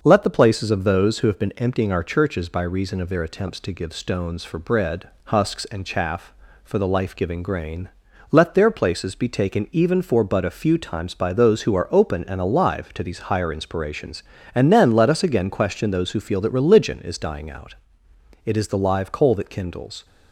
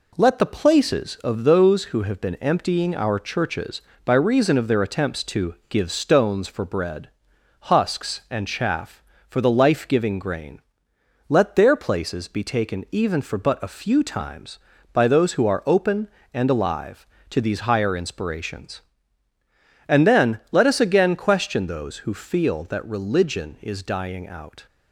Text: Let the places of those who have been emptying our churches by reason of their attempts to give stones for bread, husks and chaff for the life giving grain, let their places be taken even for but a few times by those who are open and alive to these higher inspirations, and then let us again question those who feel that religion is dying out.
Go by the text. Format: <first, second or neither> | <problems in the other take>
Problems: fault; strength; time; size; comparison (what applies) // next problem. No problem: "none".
second | starts louder than the rest; noticeable; until 1.0 s; 6 dB // goes on to say "It is the live coal that kindles"; from 18.4 s on; 1.6 s long